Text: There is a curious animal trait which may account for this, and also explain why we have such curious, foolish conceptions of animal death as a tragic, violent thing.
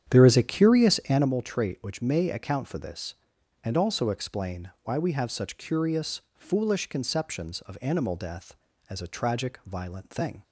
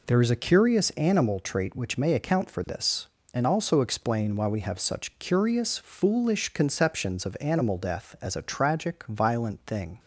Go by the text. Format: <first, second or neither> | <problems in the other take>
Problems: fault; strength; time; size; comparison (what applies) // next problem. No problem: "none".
second | starts louder than the rest; strong; until 1.3 s; 9 dB